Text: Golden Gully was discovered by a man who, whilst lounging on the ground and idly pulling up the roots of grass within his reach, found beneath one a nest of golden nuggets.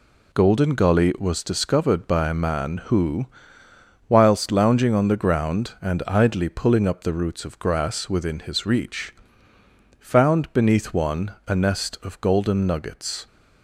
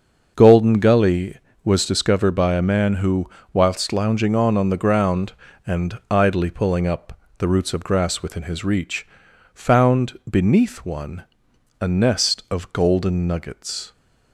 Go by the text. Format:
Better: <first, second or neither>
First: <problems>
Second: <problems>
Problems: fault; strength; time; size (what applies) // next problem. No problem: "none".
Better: first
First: none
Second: starts louder than the rest; until 1.3 s; 6 dB // says "on" twice; at 4.5 s // pauses between "up" and "the"; slight; at 7.1 s; 0.20 s long // pauses between "one" and "a"; noticeable; at 11.2 s; 0.56 s long